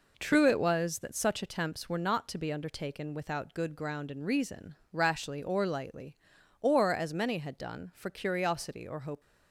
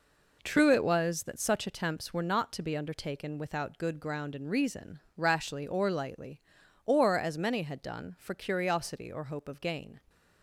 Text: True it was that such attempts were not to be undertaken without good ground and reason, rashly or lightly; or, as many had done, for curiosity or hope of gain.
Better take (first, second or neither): second